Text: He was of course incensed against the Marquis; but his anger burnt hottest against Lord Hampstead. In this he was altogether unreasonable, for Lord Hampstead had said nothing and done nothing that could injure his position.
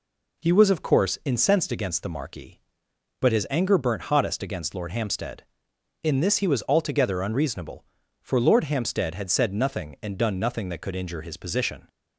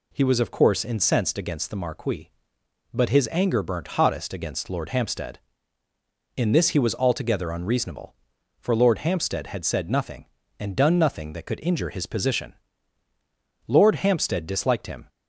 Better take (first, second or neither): first